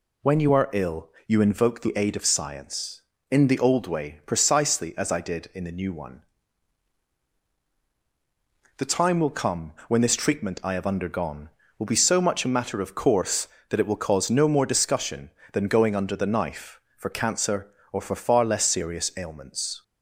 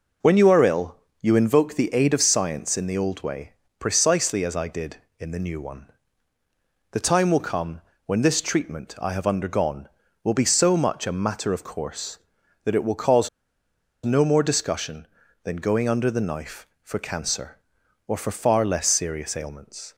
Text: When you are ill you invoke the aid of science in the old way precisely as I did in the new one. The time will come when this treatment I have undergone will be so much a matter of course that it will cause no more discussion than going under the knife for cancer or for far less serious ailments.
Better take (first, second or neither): first